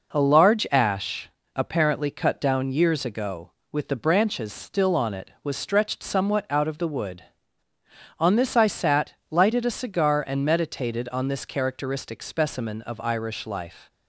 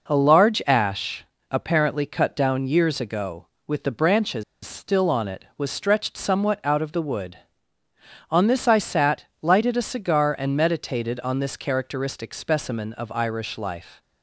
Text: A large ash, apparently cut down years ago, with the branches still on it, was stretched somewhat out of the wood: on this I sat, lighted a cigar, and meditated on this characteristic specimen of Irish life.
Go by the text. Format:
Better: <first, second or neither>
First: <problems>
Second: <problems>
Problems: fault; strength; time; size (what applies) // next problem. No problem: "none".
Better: first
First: none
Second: pauses between "branches" and "still"; slight; at 4.4 s; 0.21 s long